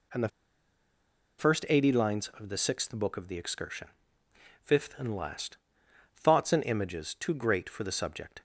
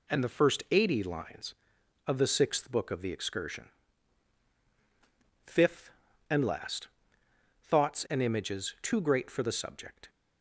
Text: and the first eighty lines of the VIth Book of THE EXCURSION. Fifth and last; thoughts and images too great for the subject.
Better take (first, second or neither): second